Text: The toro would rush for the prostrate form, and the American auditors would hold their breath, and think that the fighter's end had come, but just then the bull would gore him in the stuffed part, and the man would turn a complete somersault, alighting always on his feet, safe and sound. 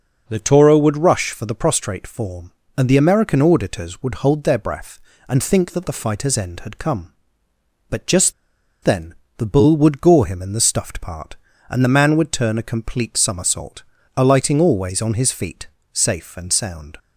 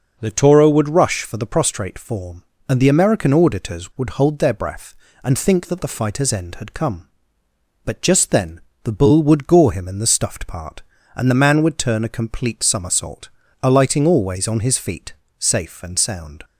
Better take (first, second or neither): second